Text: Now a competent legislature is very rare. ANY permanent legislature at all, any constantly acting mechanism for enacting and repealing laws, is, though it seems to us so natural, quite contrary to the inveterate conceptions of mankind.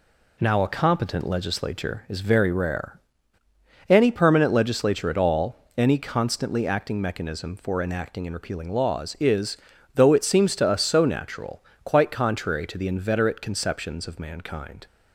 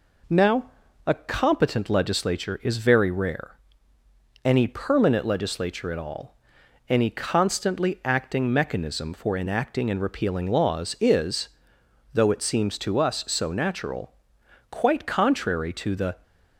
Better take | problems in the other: first | pauses between "Now" and "a"; slight; at 0.7 s; 0.36 s long // stops before "inveterate conceptions of mankind"; at 16.2 s

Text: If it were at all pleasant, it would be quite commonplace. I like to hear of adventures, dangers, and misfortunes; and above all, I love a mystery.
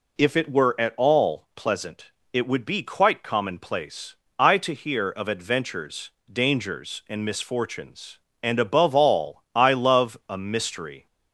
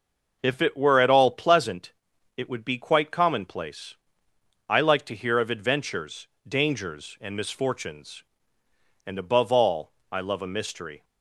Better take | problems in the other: second | skips "like"; at 4.5 s

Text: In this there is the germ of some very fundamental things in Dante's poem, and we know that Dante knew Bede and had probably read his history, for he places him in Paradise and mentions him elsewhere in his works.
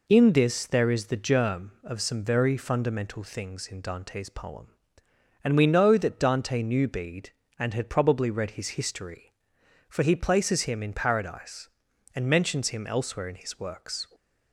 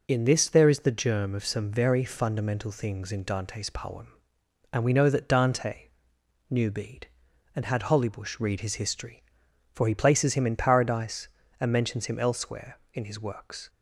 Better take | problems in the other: first | pauses between "Dante" and "knew"; noticeable; at 5.8 s; 0.62 s long // says "hollybush" for "probably"; at 7.8 s

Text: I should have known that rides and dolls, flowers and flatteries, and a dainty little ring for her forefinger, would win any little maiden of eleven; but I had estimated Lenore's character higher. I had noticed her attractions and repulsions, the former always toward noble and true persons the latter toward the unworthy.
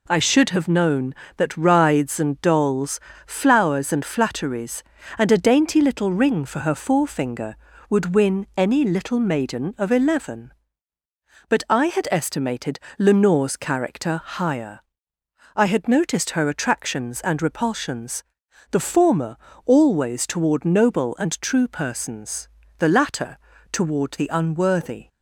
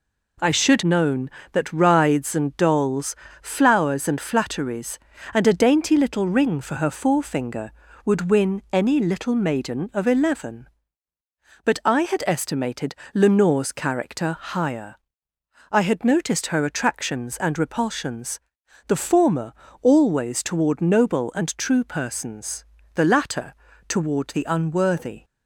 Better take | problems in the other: first | skips "have"; at 0.8 s // pauses between "estimated" and "Lenore's"; slight; at 12.9 s; 0.20 s long; slight in the first // pauses between "former" and "always"; slight; at 19.5 s; 0.26 s long; slight in the first // pauses between "persons" and "the"; slight; at 22.6 s; 0.30 s long; slight in the first // pauses between "latter" and "toward"; slight; at 23.5 s; 0.34 s long; slight in the first

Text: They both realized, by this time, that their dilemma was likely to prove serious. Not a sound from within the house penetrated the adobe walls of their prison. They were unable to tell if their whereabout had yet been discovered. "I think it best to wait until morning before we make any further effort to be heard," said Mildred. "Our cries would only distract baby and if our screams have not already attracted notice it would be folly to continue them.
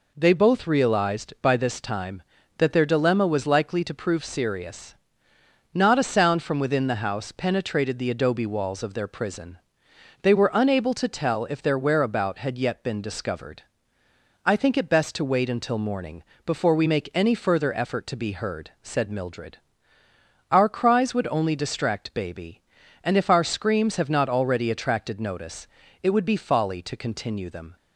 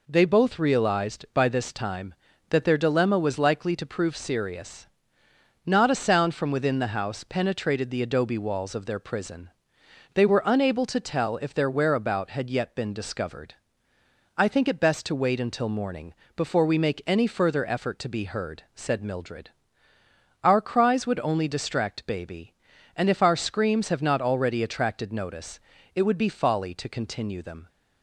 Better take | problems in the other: neither | pauses between "morning" and "before"; slight; the same in both // pauses between "notice" and "it"; slight; the same in both

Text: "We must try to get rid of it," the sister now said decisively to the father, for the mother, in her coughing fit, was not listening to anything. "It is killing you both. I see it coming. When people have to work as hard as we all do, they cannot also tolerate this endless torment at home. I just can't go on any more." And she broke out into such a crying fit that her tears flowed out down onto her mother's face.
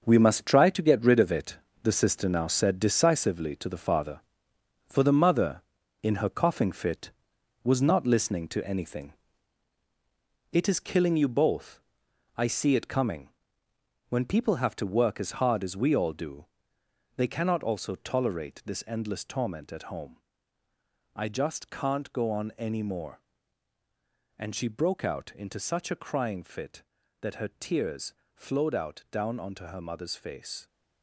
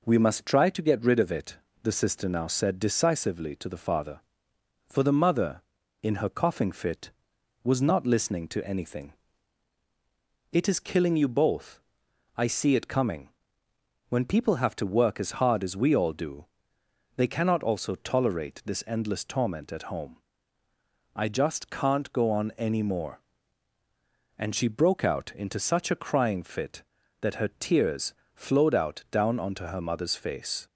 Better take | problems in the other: second | gets quieter; strong; throughout; 8 dB // pauses between "tears" and "flowed"; slight; at 28.1 s; 0.22 s long; slight in the second

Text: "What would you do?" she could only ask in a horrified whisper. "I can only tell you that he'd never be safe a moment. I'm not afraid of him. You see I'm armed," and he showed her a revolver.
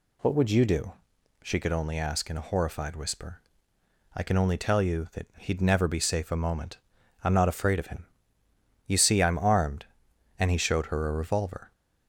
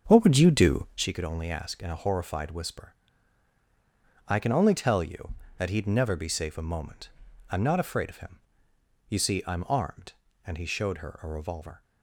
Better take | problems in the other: first | starts louder than the rest; until 1.2 s; 6.5 dB

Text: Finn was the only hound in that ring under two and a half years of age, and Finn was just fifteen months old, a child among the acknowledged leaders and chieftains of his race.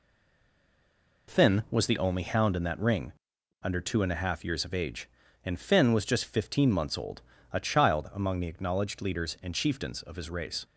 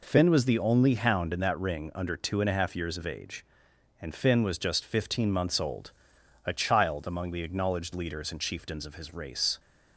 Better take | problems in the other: second | stays silent before the first word; noticeable; until 1.2 s; 1.2 s long // pauses between "ring" and "under"; noticeable; at 3.1 s; 0.48 s long

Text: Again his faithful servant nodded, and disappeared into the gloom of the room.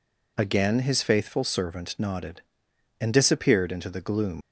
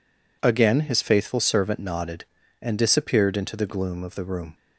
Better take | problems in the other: second | stops before "of the room"; at 4.4 s

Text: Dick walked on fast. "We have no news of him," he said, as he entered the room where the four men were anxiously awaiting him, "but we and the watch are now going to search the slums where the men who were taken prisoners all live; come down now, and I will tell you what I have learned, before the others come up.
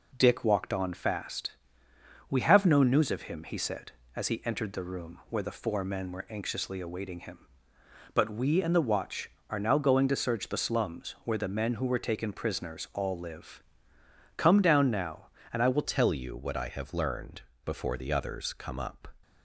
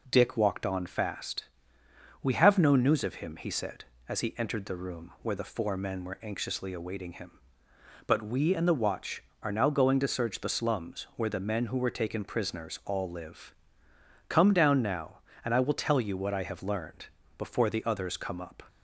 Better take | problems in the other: second | changes voice at "tell"; from 15.8 s on; 3.2 s long

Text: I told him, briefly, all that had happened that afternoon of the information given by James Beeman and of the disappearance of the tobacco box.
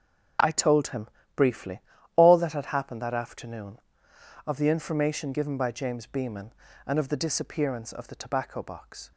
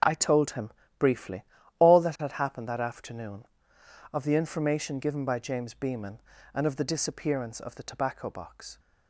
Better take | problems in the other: neither | starts louder than the rest; the same in both

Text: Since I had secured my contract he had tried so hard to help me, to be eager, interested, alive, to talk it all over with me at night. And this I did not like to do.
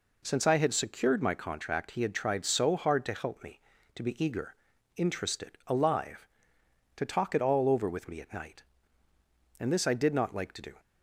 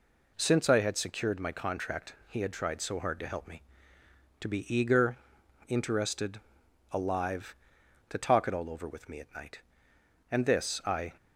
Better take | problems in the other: first | stops before "did not like to do"; at 11.1 s

